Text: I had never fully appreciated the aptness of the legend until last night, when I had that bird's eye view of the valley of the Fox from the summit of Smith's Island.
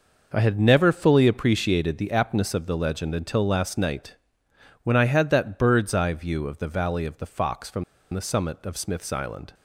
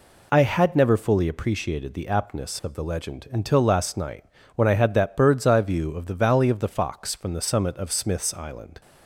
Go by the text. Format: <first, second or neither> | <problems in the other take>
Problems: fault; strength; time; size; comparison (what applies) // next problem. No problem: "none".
second | pauses between "from" and "the"; slight; at 7.8 s; 0.29 s long